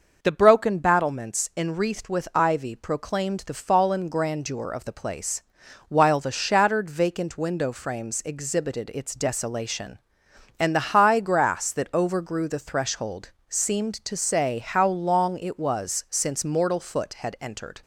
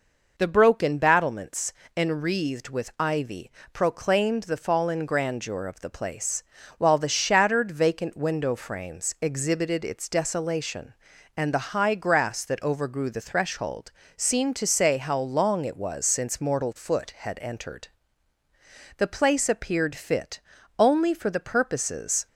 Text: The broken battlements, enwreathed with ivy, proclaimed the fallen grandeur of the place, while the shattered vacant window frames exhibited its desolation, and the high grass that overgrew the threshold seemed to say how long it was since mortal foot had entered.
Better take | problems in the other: first | pauses between "threshold" and "seemed"; slight; at 13.9 s; 0.26 s long; slight in the first // goes on to say "The place appeared fit only for the purposes"; strong; from 18.9 s on; 3.3 s long

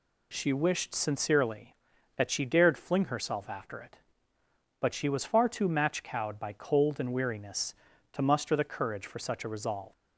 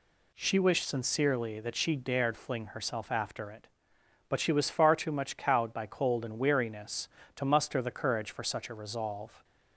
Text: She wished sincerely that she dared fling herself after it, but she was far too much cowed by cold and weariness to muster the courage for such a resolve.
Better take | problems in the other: second | says "match" for "much"; at 5.6 s

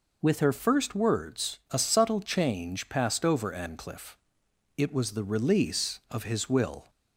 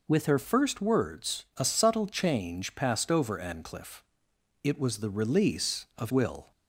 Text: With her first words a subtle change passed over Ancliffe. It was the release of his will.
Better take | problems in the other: first | skips "his"; at 6.1 s

